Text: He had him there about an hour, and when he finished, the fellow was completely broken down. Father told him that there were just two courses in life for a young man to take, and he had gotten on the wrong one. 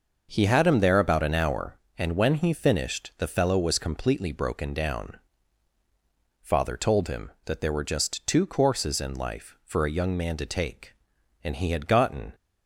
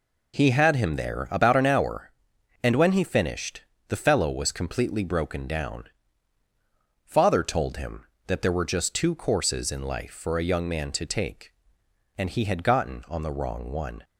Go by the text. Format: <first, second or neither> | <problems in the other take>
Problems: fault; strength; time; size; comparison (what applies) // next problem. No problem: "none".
second | stops before "on the wrong one"; at 12.3 s